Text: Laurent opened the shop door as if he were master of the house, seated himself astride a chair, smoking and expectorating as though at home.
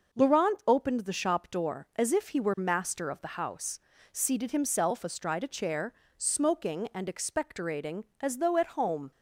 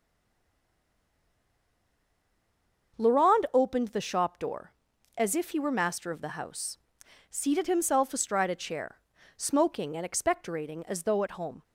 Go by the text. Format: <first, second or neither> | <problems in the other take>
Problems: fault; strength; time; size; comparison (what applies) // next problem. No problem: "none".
first | stays silent before the first word; strong; until 2.9 s; 2.9 s long // starts louder than the rest; until 4.0 s; 6.5 dB